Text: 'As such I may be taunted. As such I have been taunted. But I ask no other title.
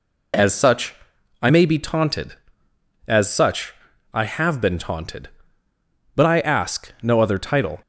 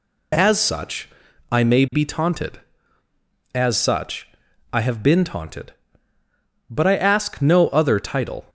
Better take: neither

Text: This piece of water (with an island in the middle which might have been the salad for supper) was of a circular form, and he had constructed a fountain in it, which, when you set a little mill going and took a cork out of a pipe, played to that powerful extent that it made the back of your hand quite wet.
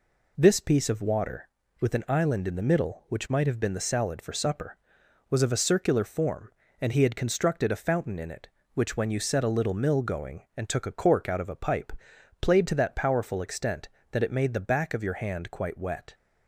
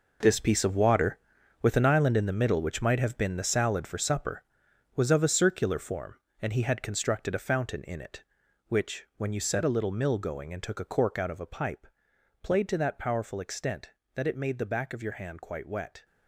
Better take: first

